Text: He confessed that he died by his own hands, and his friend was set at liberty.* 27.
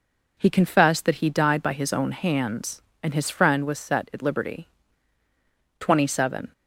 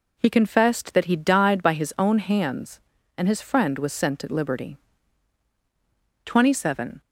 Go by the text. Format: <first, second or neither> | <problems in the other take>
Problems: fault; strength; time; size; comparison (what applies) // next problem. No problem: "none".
first | says "sent" for "set"; at 3.9 s